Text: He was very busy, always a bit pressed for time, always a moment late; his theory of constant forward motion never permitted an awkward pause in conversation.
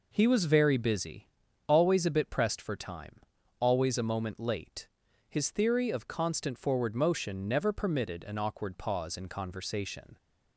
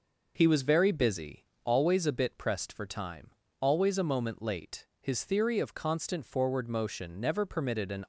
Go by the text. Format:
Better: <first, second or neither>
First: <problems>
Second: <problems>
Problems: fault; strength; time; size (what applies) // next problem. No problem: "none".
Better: first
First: none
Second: stops before "awkward pause in conversation"; at 8.0 s